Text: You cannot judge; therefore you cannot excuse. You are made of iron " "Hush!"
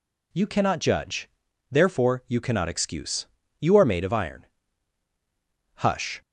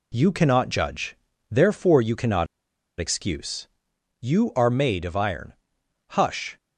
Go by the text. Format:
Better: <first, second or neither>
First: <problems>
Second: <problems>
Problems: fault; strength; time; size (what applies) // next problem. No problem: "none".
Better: first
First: none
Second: pauses between "cannot" and "excuse"; noticeable; at 2.4 s; 0.52 s long